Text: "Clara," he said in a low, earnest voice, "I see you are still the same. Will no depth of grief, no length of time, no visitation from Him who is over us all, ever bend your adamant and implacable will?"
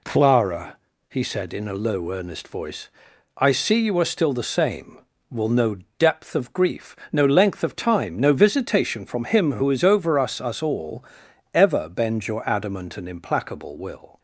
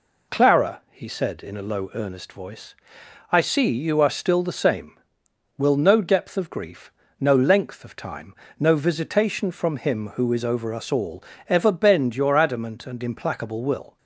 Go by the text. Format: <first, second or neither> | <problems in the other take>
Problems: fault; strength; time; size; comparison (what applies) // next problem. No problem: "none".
second | pauses between "no" and "depth"; slight; at 5.7 s; 0.22 s long // says "us" twice; at 10.4 s